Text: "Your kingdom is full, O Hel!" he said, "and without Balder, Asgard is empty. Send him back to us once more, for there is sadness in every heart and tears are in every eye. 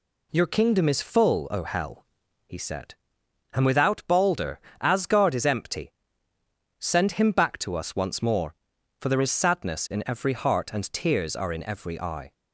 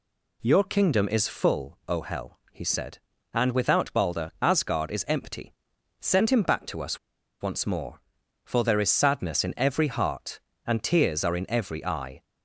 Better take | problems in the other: first | pauses between "us" and "once"; at 6.9 s; 0.42 s long

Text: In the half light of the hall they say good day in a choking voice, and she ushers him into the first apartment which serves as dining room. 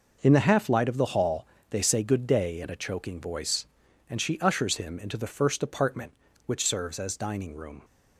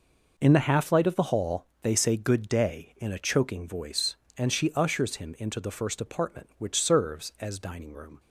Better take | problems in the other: neither | pauses between "hall" and "they"; slight; the same in both

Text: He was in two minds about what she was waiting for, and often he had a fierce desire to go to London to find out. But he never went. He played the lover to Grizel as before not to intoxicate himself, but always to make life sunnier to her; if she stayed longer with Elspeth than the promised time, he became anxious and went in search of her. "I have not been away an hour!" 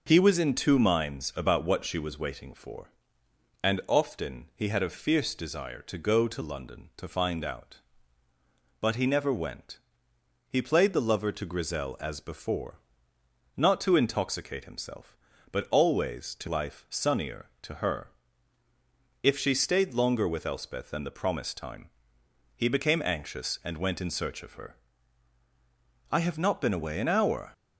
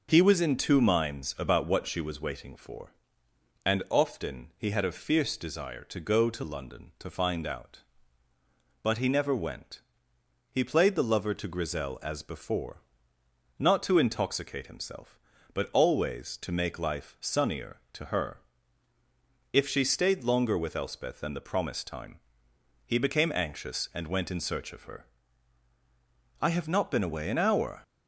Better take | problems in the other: second | pauses between "before" and "not"; noticeable; at 12.7 s; 0.78 s long; noticeable in the second // skips "make"; at 16.4 s

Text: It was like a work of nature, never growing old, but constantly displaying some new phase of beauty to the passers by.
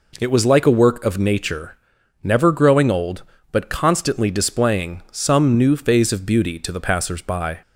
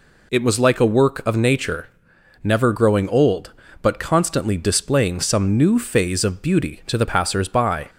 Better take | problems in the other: neither | none

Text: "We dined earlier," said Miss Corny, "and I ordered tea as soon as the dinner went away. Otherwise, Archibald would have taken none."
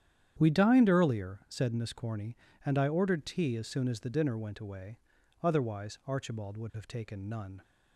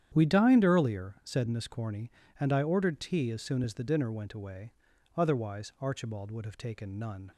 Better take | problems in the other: neither | starts louder than the rest; strong; the same in both

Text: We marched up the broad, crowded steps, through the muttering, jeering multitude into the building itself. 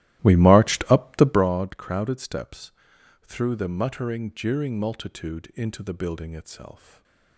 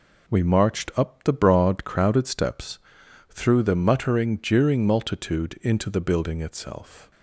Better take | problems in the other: second | starts louder than the rest; strong; until 1.4 s; 15 dB // stays silent after the last word; slight; from 6.7 s on; 0.6 s long

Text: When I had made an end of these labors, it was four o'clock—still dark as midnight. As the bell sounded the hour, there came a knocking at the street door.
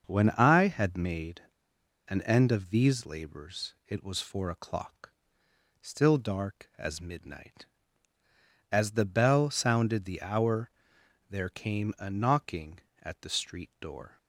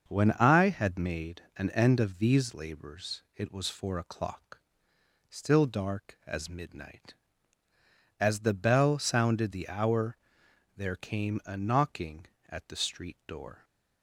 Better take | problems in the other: second | starts louder than the rest; until 1.1 s; 6.5 dB; also in the second // pauses between "made" and "an"; noticeable; at 1.4 s; 0.66 s long

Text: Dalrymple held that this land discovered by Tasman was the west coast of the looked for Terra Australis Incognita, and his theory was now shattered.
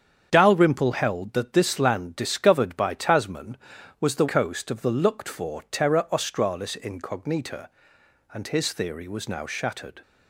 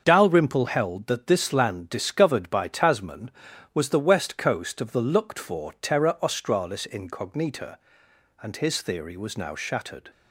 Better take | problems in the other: second | starts louder than the rest; strong; until 1.3 s; 8 dB; also in the second // skips "west"; at 4.2 s

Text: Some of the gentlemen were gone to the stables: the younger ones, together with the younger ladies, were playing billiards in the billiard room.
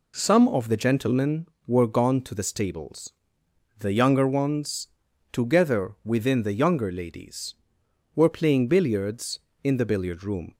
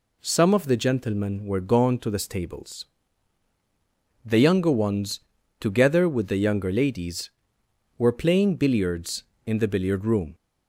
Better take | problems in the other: second | says "within" for "with"; at 6.0 s

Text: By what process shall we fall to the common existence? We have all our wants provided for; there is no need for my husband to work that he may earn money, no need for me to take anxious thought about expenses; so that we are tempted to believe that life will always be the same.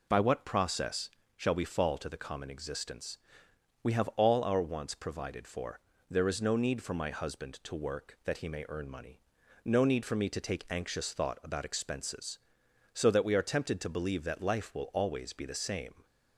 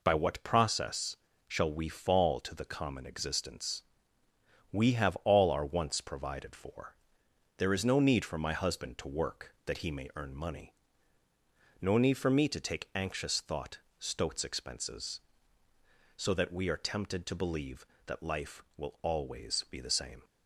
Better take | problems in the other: first | pauses between "process" and "shall"; slight; at 1.1 s; 0.32 s long; slight in the first // says "stoats" for "about"; at 13.9 s

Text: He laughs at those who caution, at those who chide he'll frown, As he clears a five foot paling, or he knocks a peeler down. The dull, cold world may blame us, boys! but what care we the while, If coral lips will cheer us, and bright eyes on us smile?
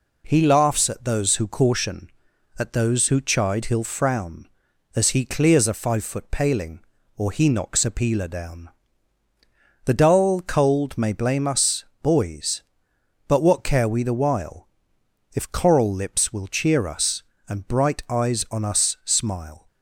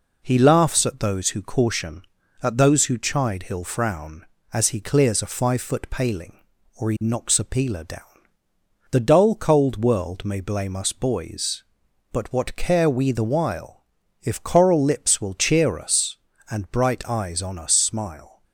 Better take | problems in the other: second | skips "world"; at 10.9 s

